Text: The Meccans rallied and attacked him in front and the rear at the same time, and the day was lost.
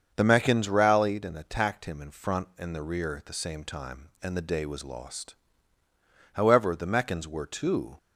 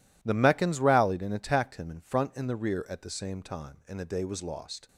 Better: second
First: starts louder than the rest; until 1.1 s; 7 dB // goes on to say "However the Meccans were too"; from 6.3 s on; 1.6 s long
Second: none

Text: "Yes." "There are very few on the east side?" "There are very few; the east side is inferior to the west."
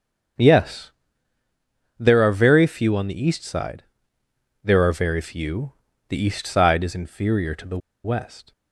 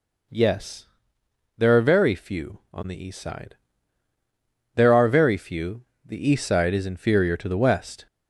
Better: second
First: starts louder than the rest; until 2.4 s; 6.5 dB // pauses between "the" and "west"; slight; at 7.7 s; 0.26 s long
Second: none

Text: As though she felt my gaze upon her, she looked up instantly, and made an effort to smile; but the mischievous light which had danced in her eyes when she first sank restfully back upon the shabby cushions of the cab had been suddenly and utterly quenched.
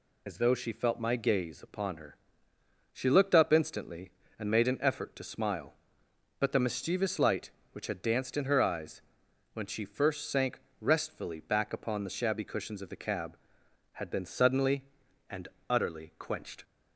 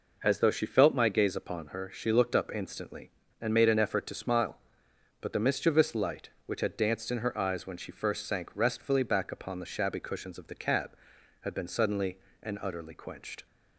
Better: second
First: loses the start of "As"; at 0.2 s; 30 ms // pauses between "eyes" and "when"; noticeable; at 9.0 s; 0.50 s long // pauses between "sank" and "restfully"; slight; at 10.5 s; 0.22 s long // pauses between "and" and "utterly"; slight; at 15.4 s; 0.20 s long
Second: none

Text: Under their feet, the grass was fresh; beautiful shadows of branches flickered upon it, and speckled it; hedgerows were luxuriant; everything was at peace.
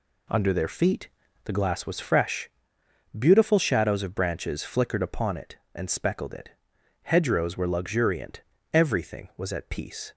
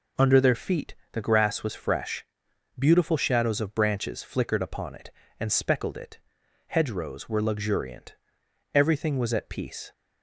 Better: second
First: says "glass" for "grass"; at 1.5 s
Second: none

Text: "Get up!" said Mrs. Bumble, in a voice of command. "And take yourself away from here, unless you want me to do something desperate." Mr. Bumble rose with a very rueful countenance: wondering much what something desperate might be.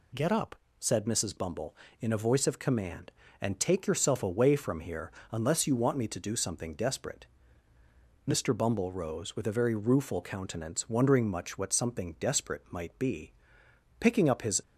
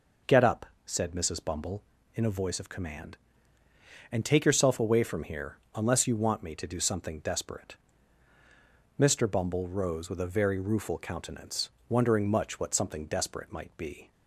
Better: second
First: goes on to say "Picking up his"; noticeable; from 13.9 s on; 0.64 s long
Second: none

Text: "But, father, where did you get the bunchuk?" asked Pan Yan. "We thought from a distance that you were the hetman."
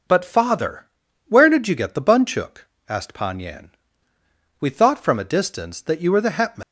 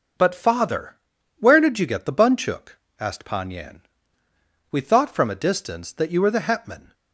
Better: second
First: leaves "hetman" unfinished; at 6.6 s; 205 ms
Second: none

